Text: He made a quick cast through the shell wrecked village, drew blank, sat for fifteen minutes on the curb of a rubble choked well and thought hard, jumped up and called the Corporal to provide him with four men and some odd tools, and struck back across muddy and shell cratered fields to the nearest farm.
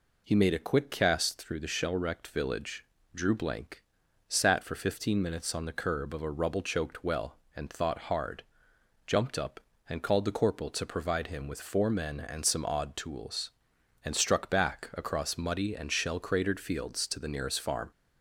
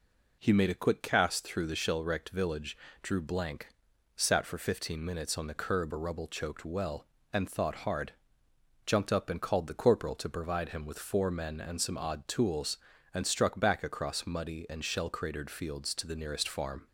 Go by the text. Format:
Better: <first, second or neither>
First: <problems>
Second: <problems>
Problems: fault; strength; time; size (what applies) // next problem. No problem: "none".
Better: first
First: none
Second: skips "of"; at 5.9 s